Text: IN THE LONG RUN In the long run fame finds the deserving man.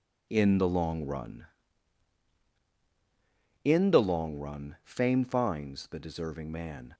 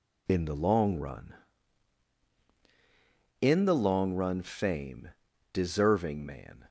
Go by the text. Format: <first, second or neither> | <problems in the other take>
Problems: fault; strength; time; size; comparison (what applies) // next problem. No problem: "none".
first | skips "finds the"; at 5.3 s